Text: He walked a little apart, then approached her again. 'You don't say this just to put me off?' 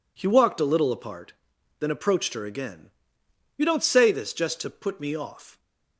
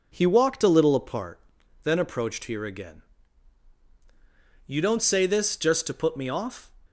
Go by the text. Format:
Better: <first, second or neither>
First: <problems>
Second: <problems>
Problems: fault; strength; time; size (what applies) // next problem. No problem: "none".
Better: first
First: none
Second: says "here" for "her"; at 2.4 s